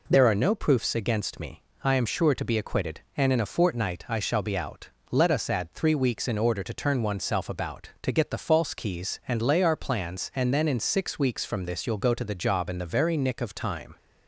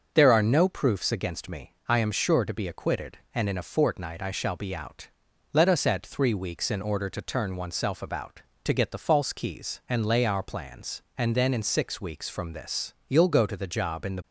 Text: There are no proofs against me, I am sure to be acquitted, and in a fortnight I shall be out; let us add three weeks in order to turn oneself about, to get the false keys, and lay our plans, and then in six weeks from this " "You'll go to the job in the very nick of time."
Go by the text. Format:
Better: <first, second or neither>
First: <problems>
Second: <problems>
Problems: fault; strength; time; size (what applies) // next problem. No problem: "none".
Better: first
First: none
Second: starts louder than the rest; until 1.1 s; 6 dB // stops before "very nick of time"; at 14.2 s